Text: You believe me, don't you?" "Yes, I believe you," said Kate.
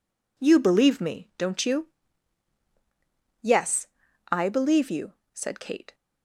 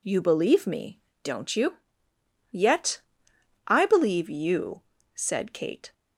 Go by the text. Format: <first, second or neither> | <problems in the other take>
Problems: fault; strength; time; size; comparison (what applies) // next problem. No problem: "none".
first | says "Yet" for "Yes"; at 2.5 s